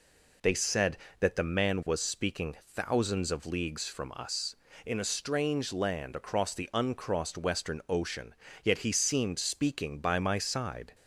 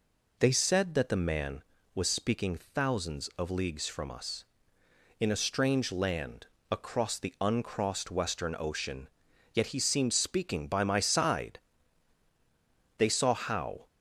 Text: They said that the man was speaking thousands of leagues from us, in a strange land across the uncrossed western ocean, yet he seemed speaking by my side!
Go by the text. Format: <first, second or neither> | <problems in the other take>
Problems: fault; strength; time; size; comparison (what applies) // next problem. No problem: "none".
first | pauses between "land" and "across"; slight; at 6.4 s; 0.24 s long // goes on to say "They saw how"; noticeable; from 12.9 s on; 0.88 s long